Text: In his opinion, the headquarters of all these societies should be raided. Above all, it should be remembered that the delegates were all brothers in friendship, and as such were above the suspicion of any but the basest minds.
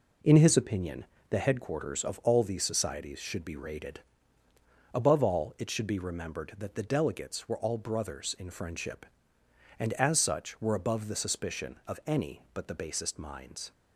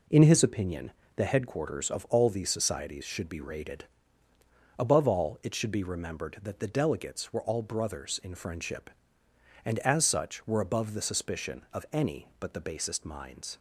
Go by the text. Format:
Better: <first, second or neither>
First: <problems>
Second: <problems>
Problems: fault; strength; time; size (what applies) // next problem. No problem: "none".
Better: neither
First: none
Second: none